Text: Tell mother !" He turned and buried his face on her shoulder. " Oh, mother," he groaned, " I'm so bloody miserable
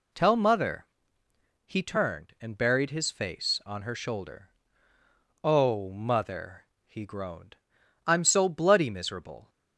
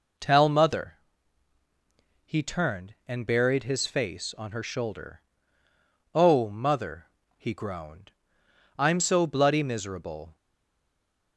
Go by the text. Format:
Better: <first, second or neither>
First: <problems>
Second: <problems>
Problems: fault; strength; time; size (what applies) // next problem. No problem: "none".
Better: first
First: none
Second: stays silent after the last word; from 10.3 s on; 1.0 s long